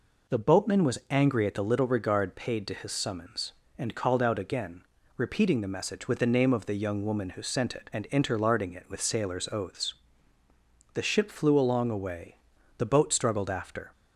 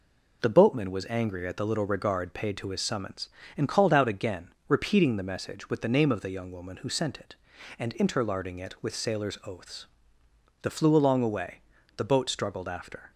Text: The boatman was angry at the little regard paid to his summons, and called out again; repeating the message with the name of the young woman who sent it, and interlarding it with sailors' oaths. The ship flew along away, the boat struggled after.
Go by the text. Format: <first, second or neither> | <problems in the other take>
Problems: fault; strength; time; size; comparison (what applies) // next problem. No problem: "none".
first | skips "ship"; at 10.7 s